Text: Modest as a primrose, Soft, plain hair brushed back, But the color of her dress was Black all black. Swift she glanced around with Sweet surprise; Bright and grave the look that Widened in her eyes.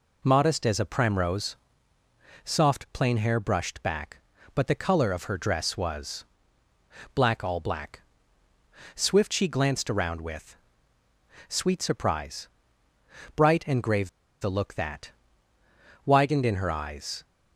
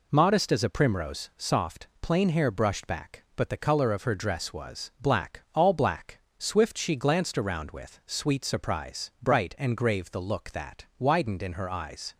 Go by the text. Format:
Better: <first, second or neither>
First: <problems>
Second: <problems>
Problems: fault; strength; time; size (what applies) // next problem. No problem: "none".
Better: second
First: pauses between "was" and "Black"; noticeable; at 6.2 s; 0.88 s long // pauses between "with" and "Sweet"; noticeable; at 10.5 s; 0.92 s long // pauses between "grave" and "the"; slight; at 14.0 s; 0.32 s long // pauses between "that" and "Widened"; noticeable; at 15.1 s; 0.92 s long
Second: none